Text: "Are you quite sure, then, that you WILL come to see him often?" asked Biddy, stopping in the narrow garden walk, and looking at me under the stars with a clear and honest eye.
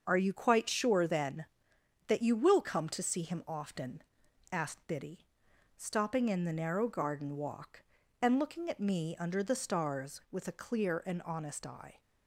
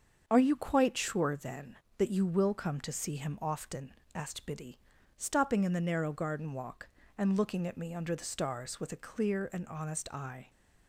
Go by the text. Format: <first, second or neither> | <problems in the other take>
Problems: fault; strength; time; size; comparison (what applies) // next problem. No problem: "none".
neither | starts louder than the rest; the same in both